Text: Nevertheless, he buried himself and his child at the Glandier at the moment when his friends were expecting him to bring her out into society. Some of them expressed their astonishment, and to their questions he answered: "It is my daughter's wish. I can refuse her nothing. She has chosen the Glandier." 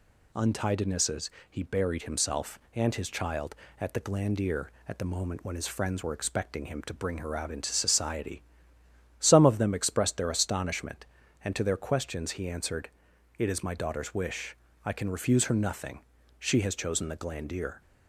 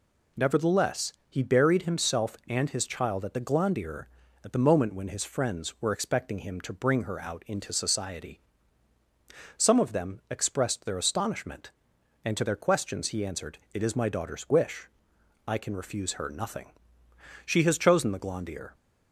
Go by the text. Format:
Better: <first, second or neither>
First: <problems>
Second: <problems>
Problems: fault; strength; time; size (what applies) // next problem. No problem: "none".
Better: second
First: says "Untidinesses" for "Nevertheless"; at 0.3 s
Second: none